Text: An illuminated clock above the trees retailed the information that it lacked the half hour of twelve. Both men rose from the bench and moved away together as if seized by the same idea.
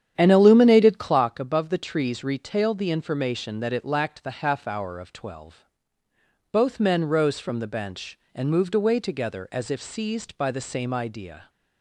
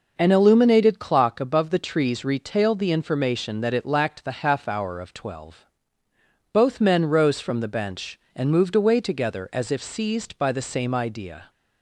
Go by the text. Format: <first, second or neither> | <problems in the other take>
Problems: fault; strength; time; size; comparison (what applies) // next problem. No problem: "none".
second | starts louder than the rest; strong; until 1.2 s; 9.5 dB